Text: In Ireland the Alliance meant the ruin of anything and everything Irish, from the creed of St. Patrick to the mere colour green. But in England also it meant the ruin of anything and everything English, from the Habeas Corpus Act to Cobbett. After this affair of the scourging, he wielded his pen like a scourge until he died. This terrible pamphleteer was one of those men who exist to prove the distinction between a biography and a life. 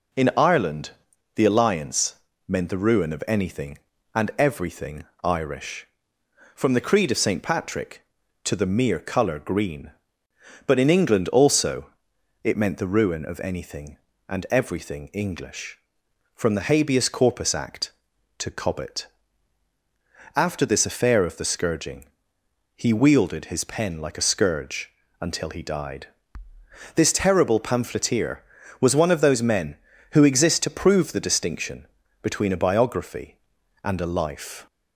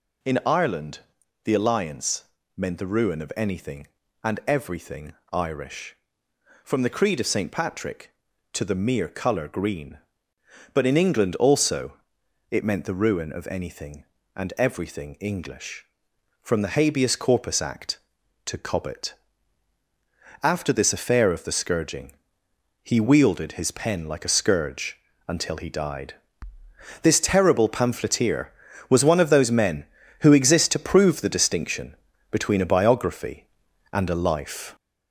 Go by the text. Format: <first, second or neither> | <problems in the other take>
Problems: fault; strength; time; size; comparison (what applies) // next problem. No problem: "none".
first | gets louder; noticeable; throughout; 5 dB // pauses between "Ireland" and "the"; noticeable; at 0.9 s; 0.46 s long; noticeable in the first // pauses between "Alliance" and "meant"; slight; at 2.2 s; 0.30 s long; slight in the first // pauses between "everything" and "Irish"; slight; at 5.1 s; 0.20 s long; slight in the first // pauses between "also" and "it"; noticeable; at 11.9 s; 0.58 s long; noticeable in the first // pauses between "scourge" and "until"; slight; at 24.9 s; 0.32 s long; slight in the first // pauses between "distinction" and "between"; slight; at 31.9 s; 0.34 s long; slight in the first